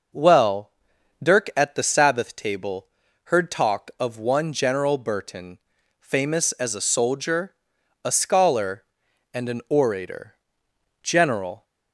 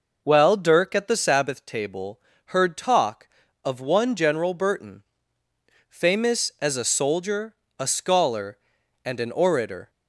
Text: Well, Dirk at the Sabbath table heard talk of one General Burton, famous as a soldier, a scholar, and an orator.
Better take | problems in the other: second | pauses between "table" and "heard"; at 2.8 s; 0.38 s long; slight in the second // goes on to say "General"; noticeable; from 11.0 s on; 0.62 s long

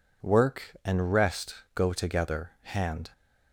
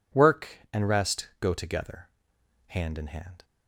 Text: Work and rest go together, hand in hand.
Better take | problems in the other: second | pauses between "rest" and "go"; slight; at 1.5 s; 0.22 s long // stops before "in hand"; at 3.1 s

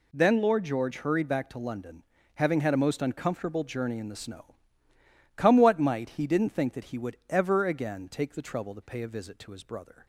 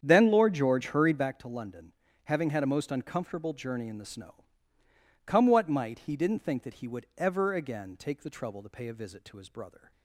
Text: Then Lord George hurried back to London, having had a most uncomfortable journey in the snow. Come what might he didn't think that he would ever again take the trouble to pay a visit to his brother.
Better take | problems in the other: first | starts louder than the rest; strong; until 1.3 s; 8 dB

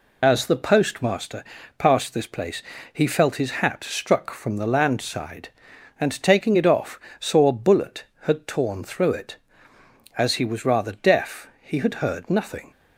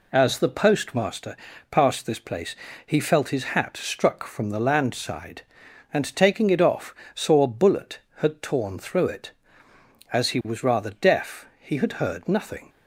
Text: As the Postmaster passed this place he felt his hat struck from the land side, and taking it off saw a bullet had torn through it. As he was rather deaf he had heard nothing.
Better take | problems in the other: second | loses the start of "As"; at 0.2 s; 35 ms // pauses between "Postmaster" and "passed"; slight; at 1.4 s; 0.34 s long; slight in the second // pauses between "place" and "he"; slight; at 2.6 s; 0.30 s long; slight in the second // pauses between "off" and "saw"; slight; at 7.0 s; 0.18 s long; slight in the second

